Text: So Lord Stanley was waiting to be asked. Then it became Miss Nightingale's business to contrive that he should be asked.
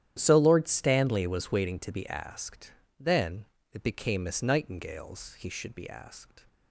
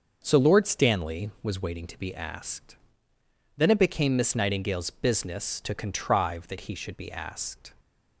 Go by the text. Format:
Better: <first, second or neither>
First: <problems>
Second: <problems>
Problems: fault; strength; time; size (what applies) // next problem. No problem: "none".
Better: second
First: starts louder than the rest; strong; until 1.2 s; 10.5 dB // pauses between "Then" and "it"; slight; at 3.4 s; 0.26 s long // skips "business to contrive that"; at 5.3 s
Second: starts louder than the rest; until 1.2 s; 6.5 dB